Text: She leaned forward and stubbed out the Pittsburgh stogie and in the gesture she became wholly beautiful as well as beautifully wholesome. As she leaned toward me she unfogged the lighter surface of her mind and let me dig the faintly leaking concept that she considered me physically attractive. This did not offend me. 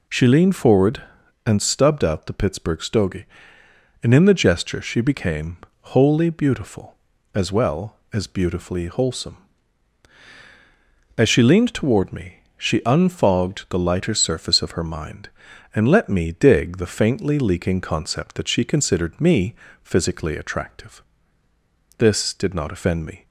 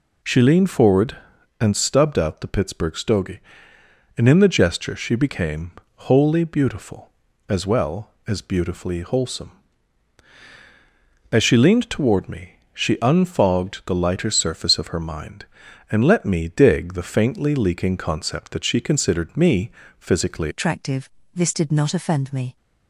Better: first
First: pauses between "became" and "wholly"; slight; at 5.5 s; 0.36 s long // pauses between "me" and "she"; slight; at 12.3 s; 0.20 s long // pauses between "me" and "physically"; slight; at 19.5 s; 0.28 s long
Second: pauses between "became" and "wholly"; slight; at 5.7 s; 0.36 s long // pauses between "me" and "she"; slight; at 12.5 s; 0.20 s long // pauses between "me" and "physically"; slight; at 19.7 s; 0.28 s long // changes voice at "attractive"; from 20.5 s on; 2.0 s long

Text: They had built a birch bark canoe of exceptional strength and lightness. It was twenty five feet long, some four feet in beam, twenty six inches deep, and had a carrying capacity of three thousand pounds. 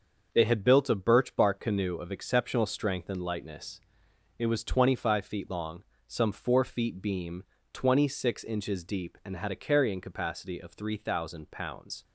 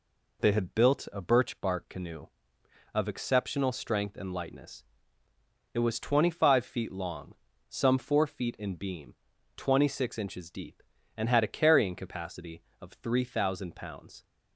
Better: second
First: starts louder than the rest; until 1.3 s; 6.5 dB // skips "in"; at 7.0 s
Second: none

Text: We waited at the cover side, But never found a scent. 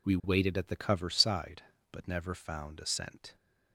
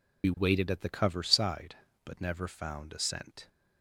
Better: first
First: none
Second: loses the start of "We"; at 0.2 s; 45 ms

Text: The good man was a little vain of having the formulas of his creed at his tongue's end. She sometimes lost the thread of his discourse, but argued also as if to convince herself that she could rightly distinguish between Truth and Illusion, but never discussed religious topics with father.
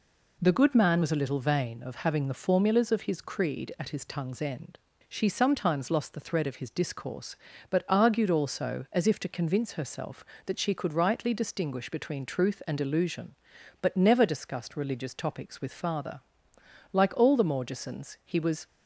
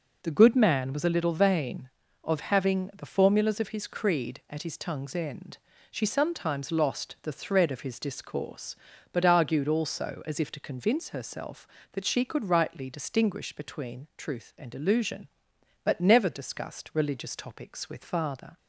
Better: second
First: goes on to say "Like all the Morgesons he was"; strong; from 16.9 s on; 1.7 s long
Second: none

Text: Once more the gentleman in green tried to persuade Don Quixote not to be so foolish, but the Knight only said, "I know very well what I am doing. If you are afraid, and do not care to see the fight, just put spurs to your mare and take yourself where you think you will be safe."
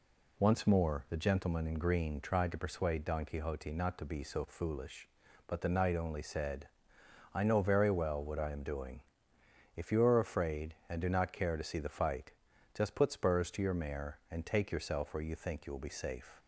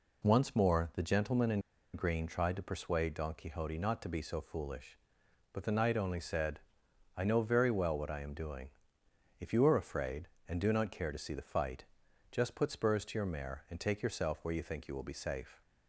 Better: first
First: none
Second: pauses between "in" and "green"; slight; at 1.5 s; 0.34 s long

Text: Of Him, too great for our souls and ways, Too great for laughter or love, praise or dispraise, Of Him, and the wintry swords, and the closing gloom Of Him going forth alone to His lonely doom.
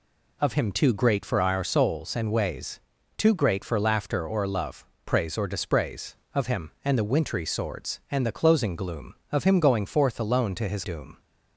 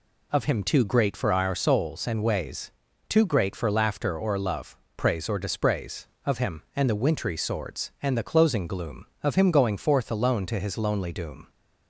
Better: second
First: skips "lonely"; at 10.8 s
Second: none

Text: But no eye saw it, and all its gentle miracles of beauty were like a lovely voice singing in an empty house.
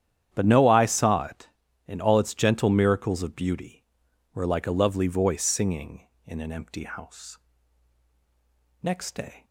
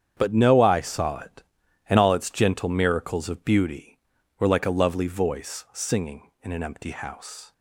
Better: second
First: starts louder than the rest; strong; until 1.3 s; 9.5 dB // goes on to say "Next day"; noticeable; from 8.8 s on; 0.62 s long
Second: starts louder than the rest; strong; until 1.1 s; 8.5 dB

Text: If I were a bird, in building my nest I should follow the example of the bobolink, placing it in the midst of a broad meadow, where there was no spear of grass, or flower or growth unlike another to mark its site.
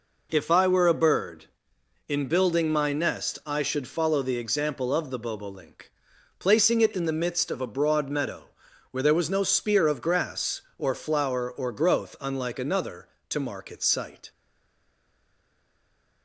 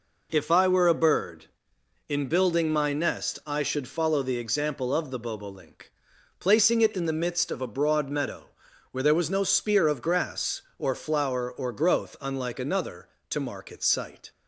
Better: second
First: stays silent after the last word; noticeable; from 14.3 s on; 1.9 s long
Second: none

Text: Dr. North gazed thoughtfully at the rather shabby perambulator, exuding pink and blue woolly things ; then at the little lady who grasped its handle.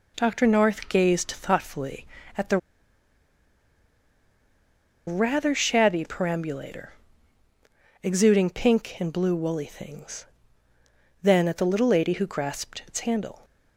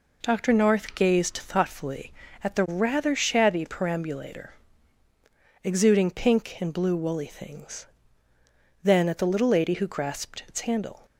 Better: second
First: pauses between "the" and "rather"; strong; at 2.5 s; 2.4 s long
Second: none

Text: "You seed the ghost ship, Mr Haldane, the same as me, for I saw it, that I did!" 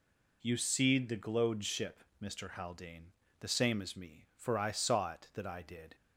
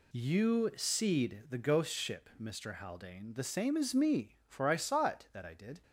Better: second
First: says "glowed" for "ghost"; at 1.1 s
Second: none

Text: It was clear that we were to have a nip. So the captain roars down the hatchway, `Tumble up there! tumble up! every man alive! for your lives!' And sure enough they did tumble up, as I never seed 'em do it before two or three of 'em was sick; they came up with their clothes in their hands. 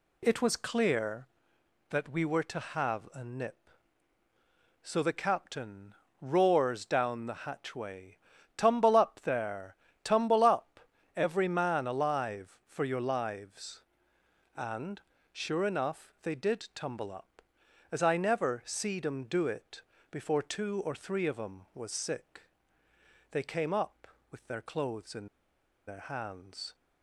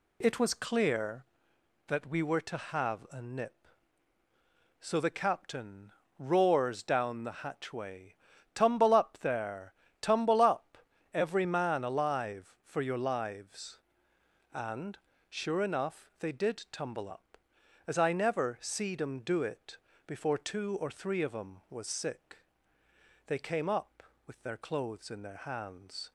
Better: second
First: pauses between "captain" and "roars"; slight; at 5.9 s; 0.28 s long // pauses between "And" and "sure"; slight; at 15.0 s; 0.32 s long // pauses between "it" and "before"; slight; at 19.8 s; 0.28 s long // pauses between "in" and "their"; noticeable; at 25.2 s; 0.61 s long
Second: pauses between "captain" and "roars"; slight; at 5.9 s; 0.28 s long // pauses between "And" and "sure"; slight; at 14.9 s; 0.32 s long // pauses between "it" and "before"; slight; at 19.7 s; 0.28 s long

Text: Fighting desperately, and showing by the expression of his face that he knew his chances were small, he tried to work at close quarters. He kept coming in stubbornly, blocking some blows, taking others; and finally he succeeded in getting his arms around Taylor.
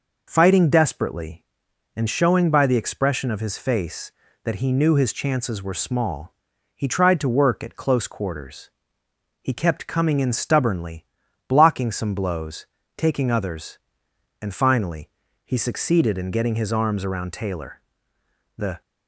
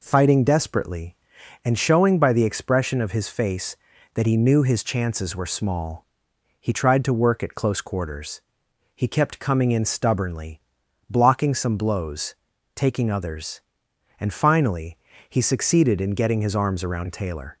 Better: second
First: pauses between "finally" and "he"; at 15.0 s; 0.38 s long // goes on to say "The"; slight; from 18.5 s on; 0.26 s long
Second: pauses between "finally" and "he"; slight; at 14.9 s; 0.32 s long

